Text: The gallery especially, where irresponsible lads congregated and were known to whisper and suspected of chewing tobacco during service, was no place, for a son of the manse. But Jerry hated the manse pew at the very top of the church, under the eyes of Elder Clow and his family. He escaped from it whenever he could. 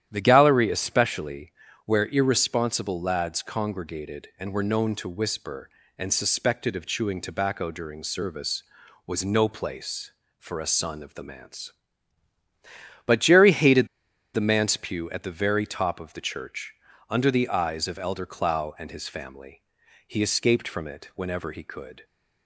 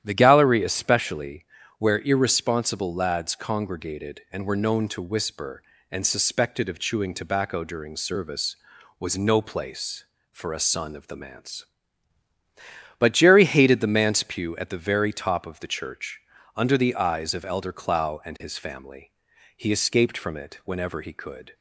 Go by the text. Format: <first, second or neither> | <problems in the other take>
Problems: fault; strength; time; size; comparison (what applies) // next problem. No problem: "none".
second | starts louder than the rest; strong; until 1.1 s; 11 dB; strong in the second // pauses between "hated" and "the"; noticeable; at 13.8 s; 0.46 s long